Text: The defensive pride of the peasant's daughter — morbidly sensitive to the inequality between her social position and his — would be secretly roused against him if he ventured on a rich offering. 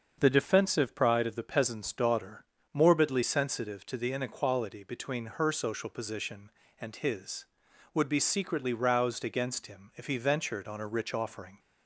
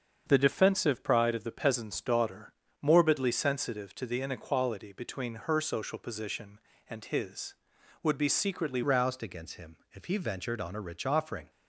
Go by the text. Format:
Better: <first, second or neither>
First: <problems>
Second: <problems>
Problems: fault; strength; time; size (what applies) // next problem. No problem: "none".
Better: first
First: starts louder than the rest; until 1.2 s; 6.5 dB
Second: starts louder than the rest; until 1.3 s; 7 dB // changes voice at "roused"; from 8.8 s on; 2.7 s long // pauses between "him" and "if"; slight; at 9.7 s; 0.16 s long